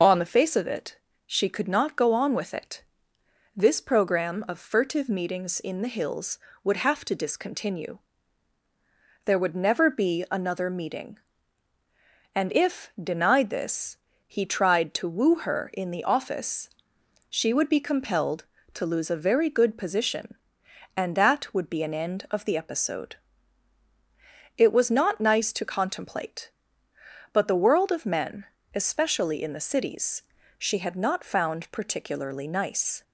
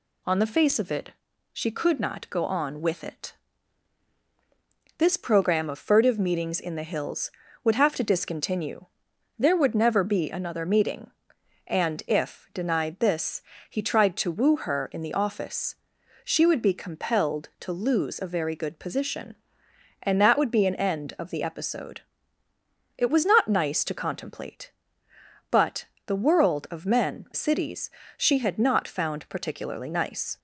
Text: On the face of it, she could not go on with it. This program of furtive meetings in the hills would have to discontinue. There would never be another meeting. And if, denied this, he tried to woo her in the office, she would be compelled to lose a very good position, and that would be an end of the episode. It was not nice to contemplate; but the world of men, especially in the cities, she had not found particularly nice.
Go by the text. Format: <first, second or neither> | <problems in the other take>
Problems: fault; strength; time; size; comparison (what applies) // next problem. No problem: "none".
first | pauses between "but" and "the"; slight; at 25.8 s; 0.20 s long // skips "especially in the"; at 27.2 s